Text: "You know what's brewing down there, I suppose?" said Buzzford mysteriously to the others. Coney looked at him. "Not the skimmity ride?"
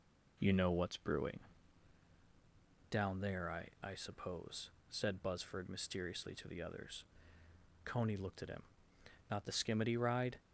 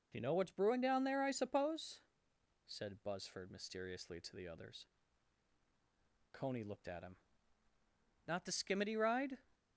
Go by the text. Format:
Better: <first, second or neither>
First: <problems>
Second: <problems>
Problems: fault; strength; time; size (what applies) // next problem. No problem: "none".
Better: second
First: pauses between "brewing" and "down"; strong; at 1.3 s; 1.5 s long // says "I" twice; at 3.8 s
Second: none